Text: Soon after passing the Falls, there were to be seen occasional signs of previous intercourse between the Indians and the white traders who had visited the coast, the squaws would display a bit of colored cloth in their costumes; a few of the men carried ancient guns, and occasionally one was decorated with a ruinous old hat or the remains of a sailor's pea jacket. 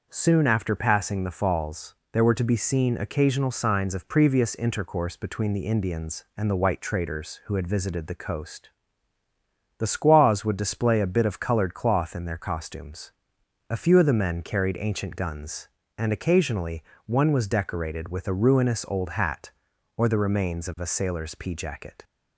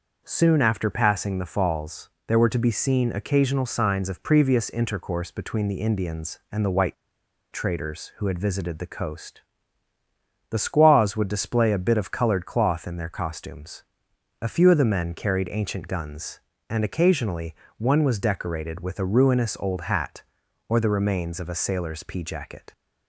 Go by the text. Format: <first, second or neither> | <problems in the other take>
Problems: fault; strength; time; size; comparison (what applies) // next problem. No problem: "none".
first | starts louder than the rest; noticeable; until 1.2 s; 6 dB; noticeable in the first // pauses between "white" and "traders"; noticeable; at 6.9 s; 0.57 s long // pauses between "occasionally" and "one"; slight; at 17.5 s; 0.24 s long; slight in the first